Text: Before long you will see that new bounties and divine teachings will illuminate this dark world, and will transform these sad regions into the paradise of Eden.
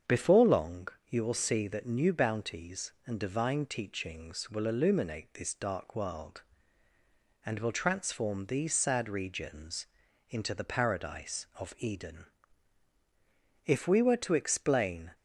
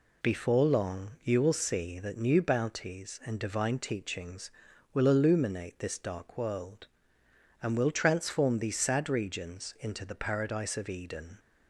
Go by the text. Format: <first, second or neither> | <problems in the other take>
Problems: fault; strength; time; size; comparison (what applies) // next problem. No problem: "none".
second | starts louder than the rest; strong; until 1.2 s; 7.5 dB // pauses between "long" and "you"; slight; at 0.8 s; 0.20 s long // pauses between "regions" and "into"; at 9.8 s; 0.42 s long // goes on to say "If we were to explain"; from 13.6 s on; 1.5 s long